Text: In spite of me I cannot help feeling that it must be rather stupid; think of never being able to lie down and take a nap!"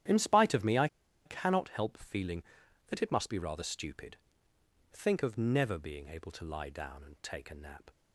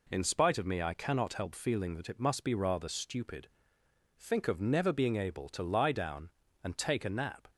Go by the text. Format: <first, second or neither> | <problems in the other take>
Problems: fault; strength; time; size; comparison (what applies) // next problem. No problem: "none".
second | starts louder than the rest; strong; until 1.4 s; 11 dB // pauses between "I" and "cannot"; at 0.8 s; 0.38 s long